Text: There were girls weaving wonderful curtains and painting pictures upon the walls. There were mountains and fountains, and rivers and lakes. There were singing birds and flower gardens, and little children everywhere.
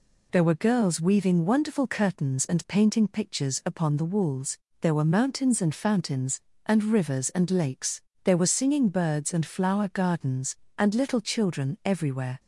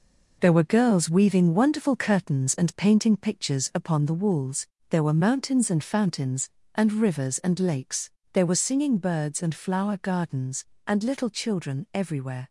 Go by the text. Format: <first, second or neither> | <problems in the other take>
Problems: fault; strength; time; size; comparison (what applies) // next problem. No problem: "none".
first | gets quieter; throughout; 7 dB